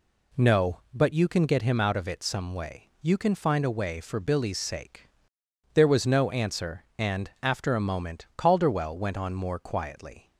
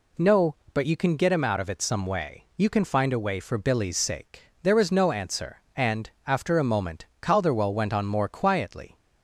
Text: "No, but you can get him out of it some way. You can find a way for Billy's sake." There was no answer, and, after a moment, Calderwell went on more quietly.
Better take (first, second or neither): neither